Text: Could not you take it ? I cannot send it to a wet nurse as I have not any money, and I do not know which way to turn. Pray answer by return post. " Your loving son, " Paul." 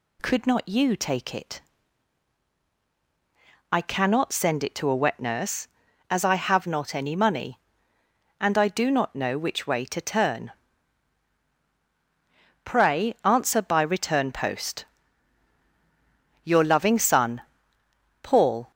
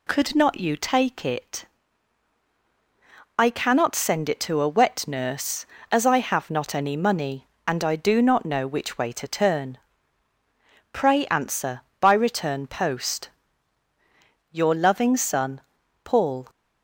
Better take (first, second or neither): neither